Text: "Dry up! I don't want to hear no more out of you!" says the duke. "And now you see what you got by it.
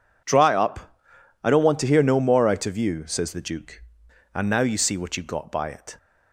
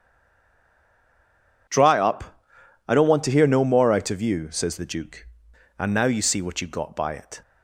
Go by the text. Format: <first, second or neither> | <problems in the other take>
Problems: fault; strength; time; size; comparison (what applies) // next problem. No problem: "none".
first | stays silent before the first word; noticeable; until 1.6 s; 1.6 s long